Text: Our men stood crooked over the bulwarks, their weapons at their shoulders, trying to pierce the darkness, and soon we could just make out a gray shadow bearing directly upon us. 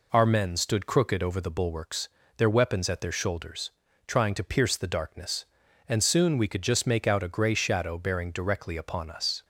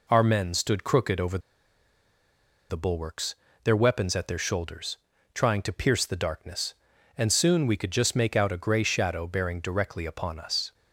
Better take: first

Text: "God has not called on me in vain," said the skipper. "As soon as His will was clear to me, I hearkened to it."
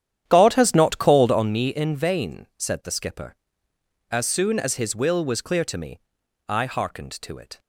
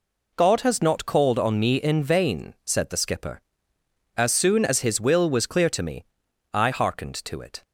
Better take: second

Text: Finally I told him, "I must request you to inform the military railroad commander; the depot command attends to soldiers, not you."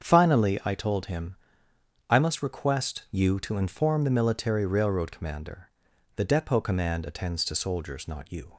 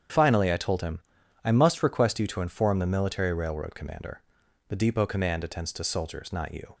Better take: neither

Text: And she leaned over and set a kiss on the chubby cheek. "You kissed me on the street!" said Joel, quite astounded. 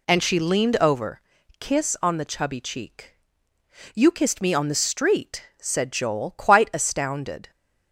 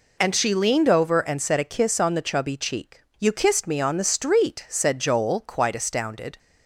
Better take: second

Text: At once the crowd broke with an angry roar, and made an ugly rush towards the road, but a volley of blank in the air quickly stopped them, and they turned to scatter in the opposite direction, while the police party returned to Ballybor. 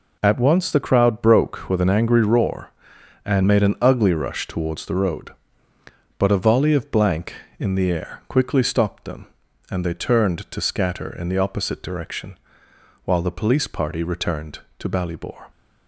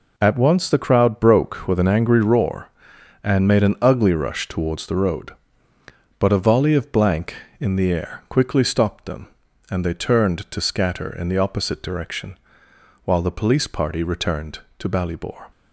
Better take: neither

